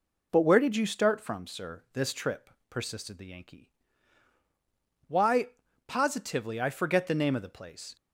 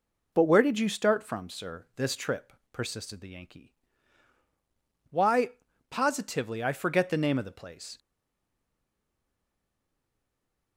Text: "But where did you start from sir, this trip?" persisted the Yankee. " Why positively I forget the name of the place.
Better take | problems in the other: first | pauses between "Why" and "positively"; at 5.5 s; 0.40 s long; also in the first // stays silent after the last word; strong; from 7.9 s on; 2.8 s long

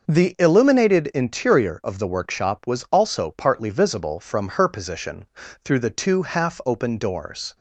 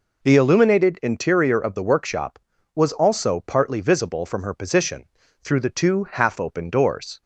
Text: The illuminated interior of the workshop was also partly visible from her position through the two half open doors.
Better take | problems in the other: neither | pauses between "position" and "through"; the same in both

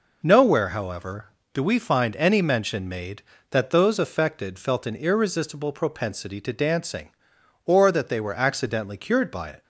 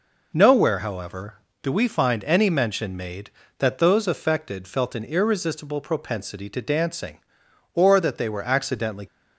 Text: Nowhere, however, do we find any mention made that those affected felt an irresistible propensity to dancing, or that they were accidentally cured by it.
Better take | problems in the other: first | stops before "cured by it"; at 9.0 s

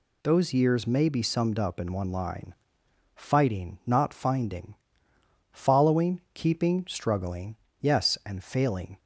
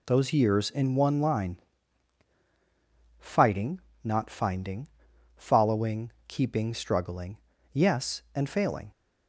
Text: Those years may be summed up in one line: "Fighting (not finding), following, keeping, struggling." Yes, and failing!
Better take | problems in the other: first | skips "may be summed up"; at 0.6 s

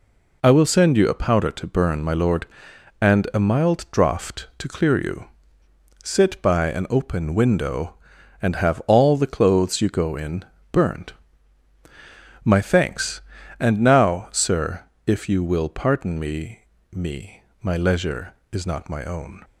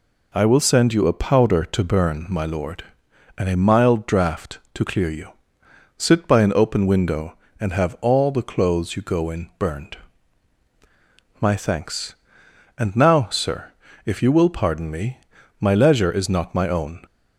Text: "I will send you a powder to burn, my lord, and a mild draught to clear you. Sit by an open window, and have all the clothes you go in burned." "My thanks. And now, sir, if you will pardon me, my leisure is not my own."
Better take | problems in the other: second | pauses between "in" and "burned"; slight; at 10.4 s; 0.28 s long // says "me" twice; at 16.9 s

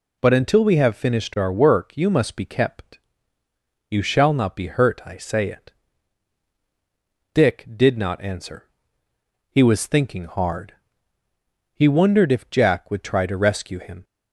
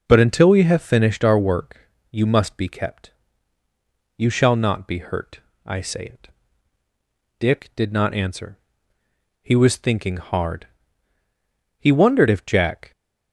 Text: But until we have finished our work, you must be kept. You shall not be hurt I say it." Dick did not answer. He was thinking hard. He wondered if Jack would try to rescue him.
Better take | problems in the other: first | pauses between "hurt" and "I"; slight; at 5.4 s; 0.26 s long // stops before "would try to rescue him"; at 12.9 s

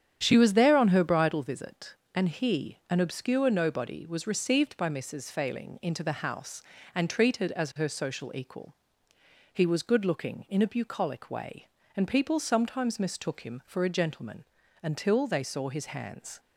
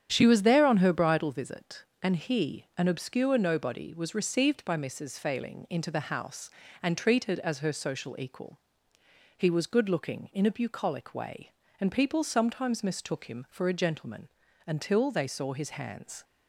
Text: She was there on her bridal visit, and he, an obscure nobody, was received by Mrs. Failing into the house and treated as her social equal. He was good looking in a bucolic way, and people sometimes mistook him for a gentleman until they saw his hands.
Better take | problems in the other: neither | starts louder than the rest; strong; the same in both // pauses between "gentleman" and "until"; slight; the same in both

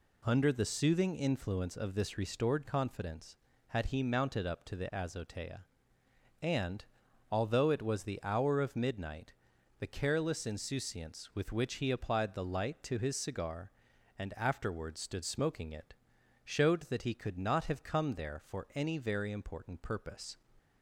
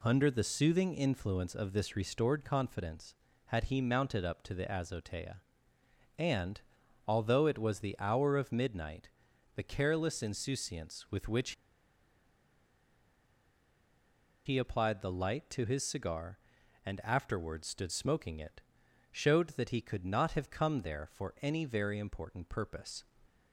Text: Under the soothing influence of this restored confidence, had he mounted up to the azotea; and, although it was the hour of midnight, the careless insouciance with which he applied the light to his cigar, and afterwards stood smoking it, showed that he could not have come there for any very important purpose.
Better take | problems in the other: first | pauses between "which" and "he"; strong; at 11.5 s; 2.9 s long

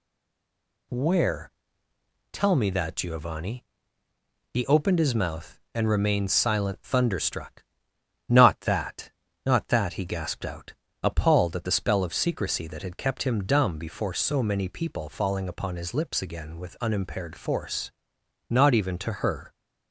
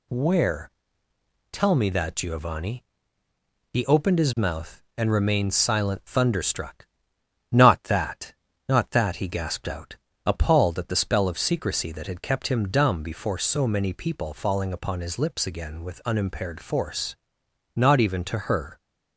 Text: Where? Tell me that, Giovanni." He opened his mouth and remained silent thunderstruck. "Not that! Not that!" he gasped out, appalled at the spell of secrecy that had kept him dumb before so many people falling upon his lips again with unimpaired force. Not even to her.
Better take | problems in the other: second | stays silent before the first word; slight; until 0.8 s; 0.8 s long

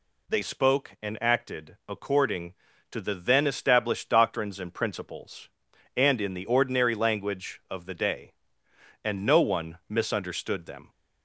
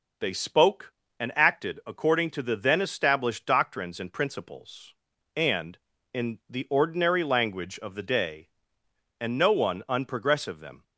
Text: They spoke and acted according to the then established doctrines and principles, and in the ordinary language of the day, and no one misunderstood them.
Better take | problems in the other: first | says "unprogressive" for "misunderstood"; at 9.8 s

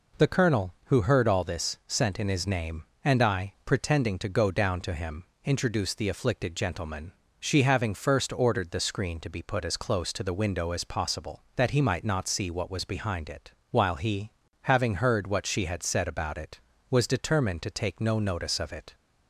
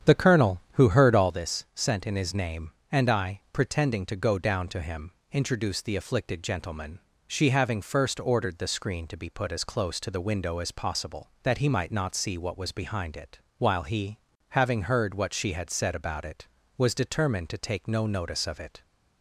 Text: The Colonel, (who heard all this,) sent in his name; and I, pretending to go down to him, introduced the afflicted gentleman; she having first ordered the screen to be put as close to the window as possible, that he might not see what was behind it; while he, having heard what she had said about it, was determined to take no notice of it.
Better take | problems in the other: first | starts louder than the rest; strong; until 1.4 s; 8.5 dB

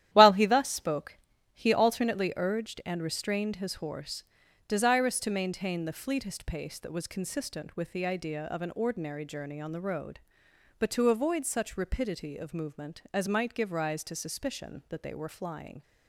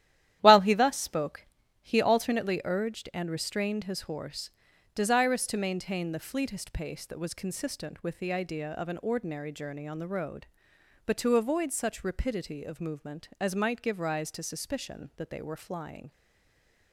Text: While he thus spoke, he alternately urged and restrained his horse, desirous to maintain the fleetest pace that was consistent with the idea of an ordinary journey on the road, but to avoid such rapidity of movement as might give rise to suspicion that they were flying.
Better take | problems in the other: first | starts louder than the rest; strong; until 1.4 s; 12 dB; strong in the first // stays silent after the last word; slight; from 16.1 s on; 0.8 s long

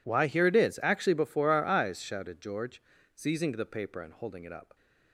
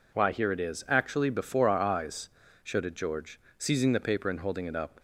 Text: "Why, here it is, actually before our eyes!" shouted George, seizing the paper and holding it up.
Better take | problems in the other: neither | none

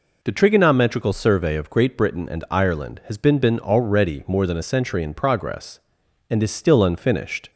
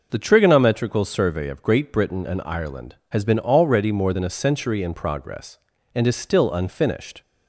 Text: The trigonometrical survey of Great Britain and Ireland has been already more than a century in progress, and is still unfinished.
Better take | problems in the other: second | says "been" twice; at 3.3 s

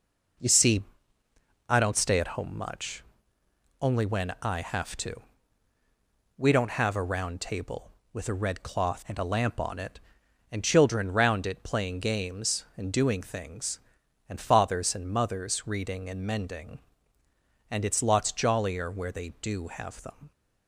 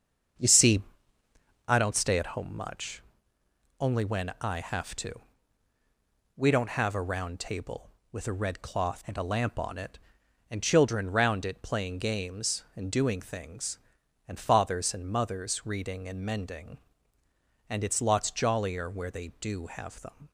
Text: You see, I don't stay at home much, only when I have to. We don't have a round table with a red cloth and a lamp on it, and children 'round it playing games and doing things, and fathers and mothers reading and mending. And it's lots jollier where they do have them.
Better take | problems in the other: first | starts louder than the rest; until 1.8 s; 7 dB

